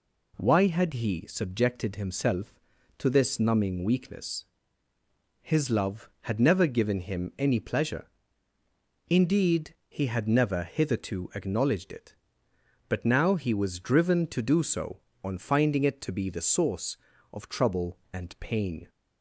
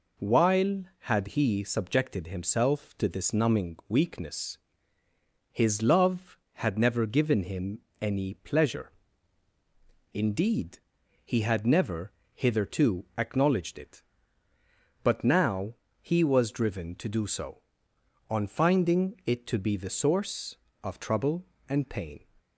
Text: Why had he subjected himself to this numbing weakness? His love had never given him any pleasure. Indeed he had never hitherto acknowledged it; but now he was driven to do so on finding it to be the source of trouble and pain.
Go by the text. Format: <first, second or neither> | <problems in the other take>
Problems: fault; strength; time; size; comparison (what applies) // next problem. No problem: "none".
first | says "While" for "Why"; at 0.1 s // pauses between "him" and "any"; slight; at 7.7 s; 0.22 s long // pauses between "Indeed" and "he"; noticeable; at 10.7 s; 0.46 s long // pauses between "never" and "hitherto"; slight; at 12.1 s; 0.22 s long // pauses between "now" and "he"; slight; at 15.7 s; 0.28 s long